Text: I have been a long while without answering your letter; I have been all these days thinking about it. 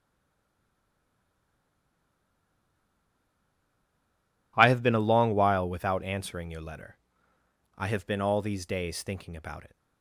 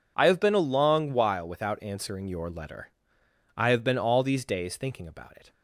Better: second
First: stays silent before the first word; strong; until 4.5 s; 4.5 s long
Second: none

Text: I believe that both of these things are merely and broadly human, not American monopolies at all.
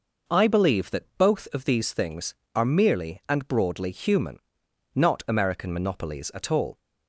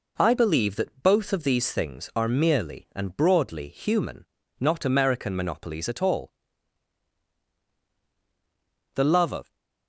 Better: first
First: none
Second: goes on to say "The love of"; noticeable; from 8.9 s on; 0.62 s long

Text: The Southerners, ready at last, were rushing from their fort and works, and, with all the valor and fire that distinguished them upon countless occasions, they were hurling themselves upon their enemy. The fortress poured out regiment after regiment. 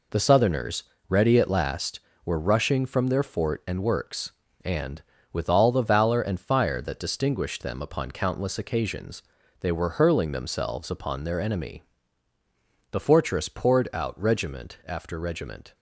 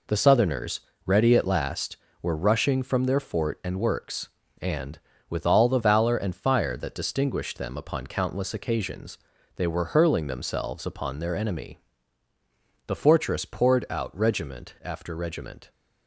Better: neither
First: none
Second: none

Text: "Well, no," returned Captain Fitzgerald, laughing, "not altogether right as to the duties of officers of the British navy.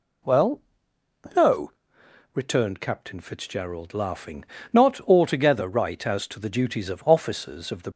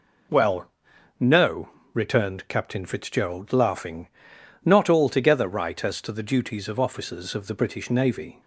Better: second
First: stops before "British navy"; at 7.9 s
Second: none

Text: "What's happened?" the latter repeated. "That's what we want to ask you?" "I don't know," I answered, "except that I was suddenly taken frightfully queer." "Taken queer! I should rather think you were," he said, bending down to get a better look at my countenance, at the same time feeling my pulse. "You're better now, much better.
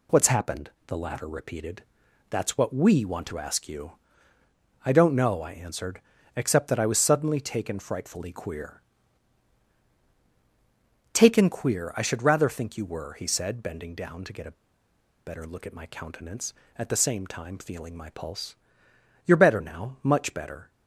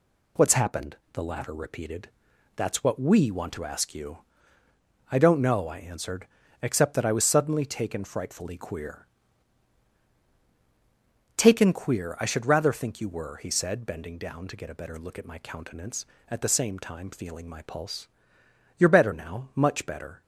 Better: second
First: pauses between "a" and "better"; noticeable; at 14.5 s; 0.72 s long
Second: none

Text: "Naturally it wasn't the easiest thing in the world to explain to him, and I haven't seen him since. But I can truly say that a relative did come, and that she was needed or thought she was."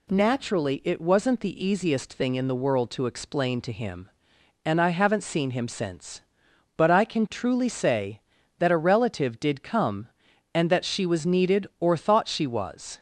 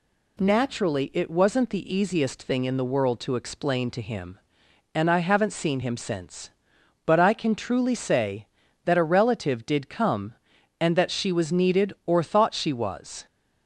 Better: neither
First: none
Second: none

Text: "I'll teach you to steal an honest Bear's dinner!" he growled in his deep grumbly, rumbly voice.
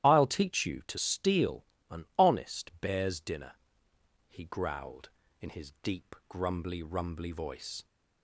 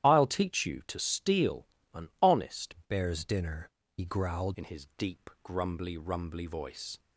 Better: first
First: starts louder than the rest; strong; until 1.0 s; 12.5 dB // pauses between "steal" and "an"; slight; at 1.6 s; 0.24 s long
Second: starts louder than the rest; strong; until 1.1 s; 12 dB // pauses between "steal" and "an"; slight; at 1.6 s; 0.26 s long // changes voice from "Bear's" to "growled"; from 2.8 to 4.5 s; 1.7 s long

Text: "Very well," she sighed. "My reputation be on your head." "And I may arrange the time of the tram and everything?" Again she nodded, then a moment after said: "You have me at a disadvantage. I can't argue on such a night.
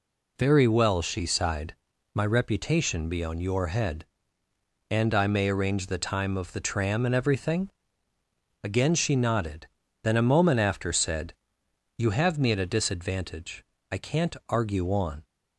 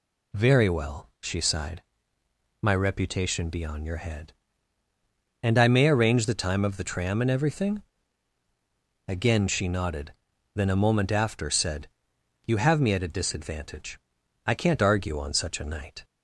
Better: second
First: stops before "such a night"; at 15.2 s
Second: none

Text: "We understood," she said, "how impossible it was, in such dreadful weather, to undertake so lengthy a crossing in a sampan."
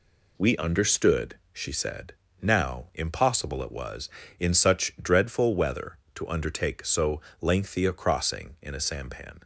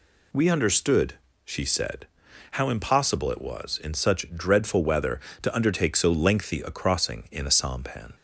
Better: second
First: says "now" for "how"; at 2.4 s // pauses between "so" and "lengthy"; slight; at 7.2 s; 0.20 s long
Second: none

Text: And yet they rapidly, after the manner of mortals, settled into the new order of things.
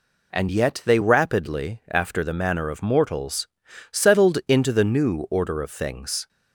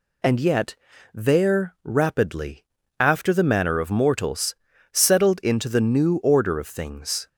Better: first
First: none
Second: says "there" for "they"; at 1.1 s

